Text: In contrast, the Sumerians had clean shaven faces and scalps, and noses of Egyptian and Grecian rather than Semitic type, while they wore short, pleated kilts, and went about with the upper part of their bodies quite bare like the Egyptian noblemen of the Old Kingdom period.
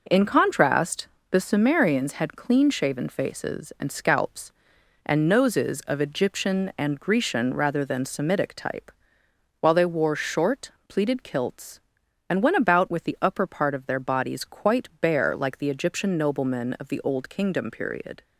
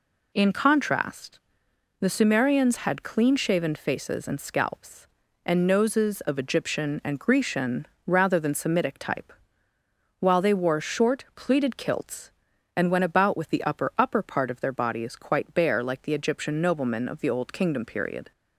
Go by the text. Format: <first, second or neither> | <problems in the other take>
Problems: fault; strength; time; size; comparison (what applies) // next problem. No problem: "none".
first | pauses between "Grecian" and "rather"; slight; at 7.8 s; 0.22 s long // says "upper" twice; at 13.9 s